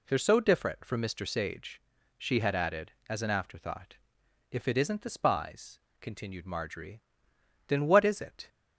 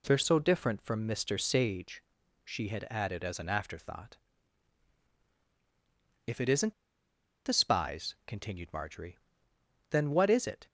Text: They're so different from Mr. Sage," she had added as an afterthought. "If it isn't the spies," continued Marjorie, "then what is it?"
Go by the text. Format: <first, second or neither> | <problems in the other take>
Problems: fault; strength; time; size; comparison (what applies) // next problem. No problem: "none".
first | pauses between "isn't" and "the"; noticeable; at 6.7 s; 0.72 s long